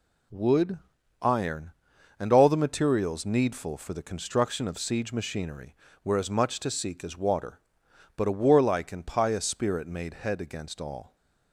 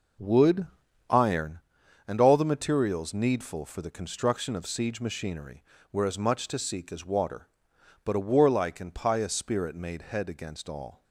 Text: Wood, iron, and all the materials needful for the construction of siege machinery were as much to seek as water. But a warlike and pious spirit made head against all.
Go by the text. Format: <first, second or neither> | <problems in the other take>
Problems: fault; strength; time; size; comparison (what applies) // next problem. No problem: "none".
first | starts louder than the rest; noticeable; until 1.6 s; 5 dB